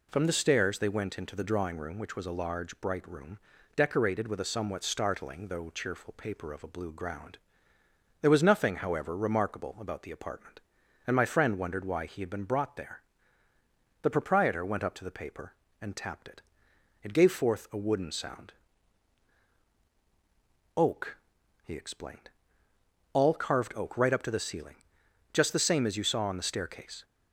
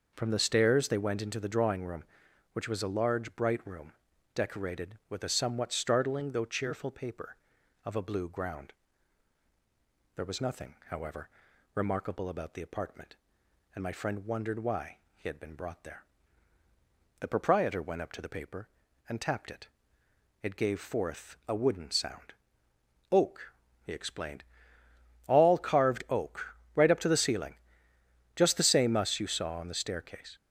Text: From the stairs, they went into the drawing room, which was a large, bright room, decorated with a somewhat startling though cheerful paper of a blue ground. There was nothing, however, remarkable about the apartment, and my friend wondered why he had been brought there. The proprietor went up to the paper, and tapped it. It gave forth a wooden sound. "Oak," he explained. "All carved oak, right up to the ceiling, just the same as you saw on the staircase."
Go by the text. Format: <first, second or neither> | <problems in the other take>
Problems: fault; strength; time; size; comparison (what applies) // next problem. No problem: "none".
first | starts louder than the rest; noticeable; until 1.1 s; 6 dB // pauses between "why" and "he"; slight; at 14.9 s; 0.16 s long // says "us" for "as"; at 28.9 s